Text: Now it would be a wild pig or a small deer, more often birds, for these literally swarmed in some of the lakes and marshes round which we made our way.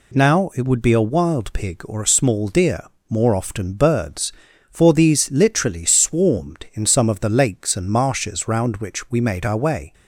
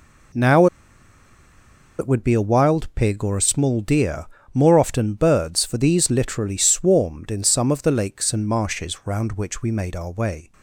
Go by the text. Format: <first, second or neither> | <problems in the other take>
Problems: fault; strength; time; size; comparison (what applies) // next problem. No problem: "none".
first | pauses between "Now" and "it"; strong; at 0.6 s; 1.3 s long